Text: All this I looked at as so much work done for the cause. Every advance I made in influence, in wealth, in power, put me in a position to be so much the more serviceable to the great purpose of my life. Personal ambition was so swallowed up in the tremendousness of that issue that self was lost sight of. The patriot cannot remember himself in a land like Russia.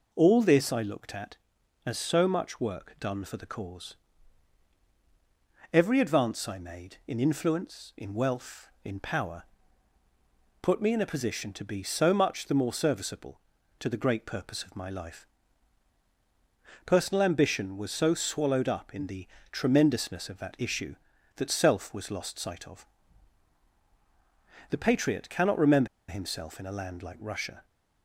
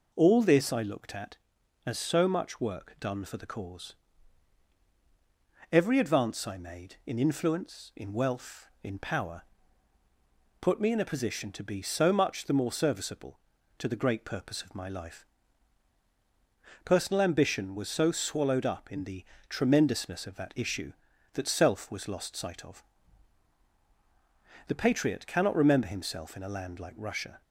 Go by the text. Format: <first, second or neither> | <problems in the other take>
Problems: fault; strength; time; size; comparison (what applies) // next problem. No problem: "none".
second | pauses between "the" and "tremendousness"; slight; at 19.2 s; 0.24 s long; slight in the second // pauses between "remember" and "himself"; slight; at 25.8 s; 0.22 s long